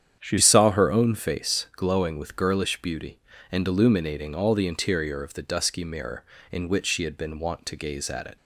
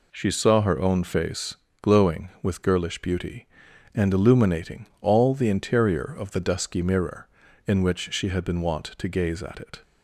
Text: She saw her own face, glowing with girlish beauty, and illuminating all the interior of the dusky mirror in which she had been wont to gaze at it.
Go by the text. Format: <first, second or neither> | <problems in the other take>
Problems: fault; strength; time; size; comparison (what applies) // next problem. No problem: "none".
second | starts louder than the rest; strong; until 1.2 s; 8.5 dB // changes voice at "saw"; from 0.4 s on; 7.9 s long